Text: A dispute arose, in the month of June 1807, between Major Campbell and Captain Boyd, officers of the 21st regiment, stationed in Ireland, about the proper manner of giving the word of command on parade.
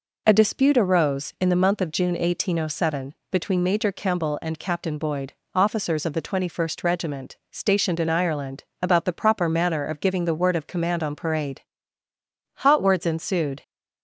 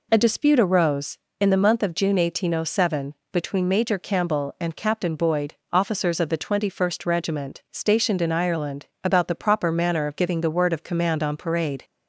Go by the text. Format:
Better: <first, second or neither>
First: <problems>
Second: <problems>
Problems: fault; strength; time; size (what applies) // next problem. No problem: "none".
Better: second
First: goes on to say "Hot words ensued"; noticeable; from 12.5 s on; 1.0 s long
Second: none